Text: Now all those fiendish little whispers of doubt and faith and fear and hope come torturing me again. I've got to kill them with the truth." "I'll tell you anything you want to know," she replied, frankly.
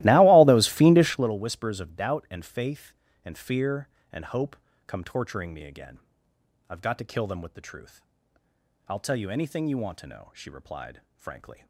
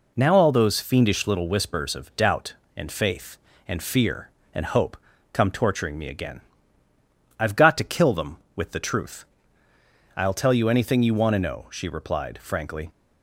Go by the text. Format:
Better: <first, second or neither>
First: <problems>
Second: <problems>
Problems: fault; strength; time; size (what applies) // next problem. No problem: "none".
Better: second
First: starts louder than the rest; strong; until 1.4 s; 17 dB // pauses between "hope" and "come"; slight; at 4.5 s; 0.32 s long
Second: pauses between "hope" and "come"; slight; at 4.9 s; 0.34 s long